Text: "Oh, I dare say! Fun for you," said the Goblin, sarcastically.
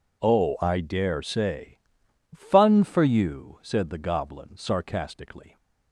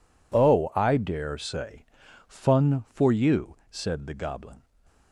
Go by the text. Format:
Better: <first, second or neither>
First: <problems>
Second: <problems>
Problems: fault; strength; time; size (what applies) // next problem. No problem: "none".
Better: first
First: none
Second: stops before "sarcastically"; at 4.8 s